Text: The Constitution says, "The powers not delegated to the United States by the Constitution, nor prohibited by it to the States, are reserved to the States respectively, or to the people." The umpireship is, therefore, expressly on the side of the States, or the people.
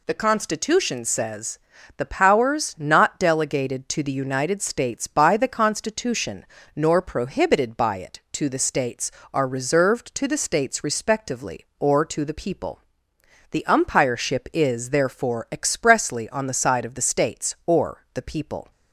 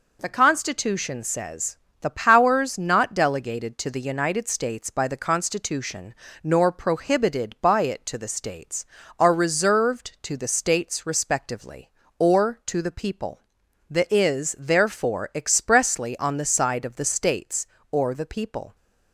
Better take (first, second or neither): first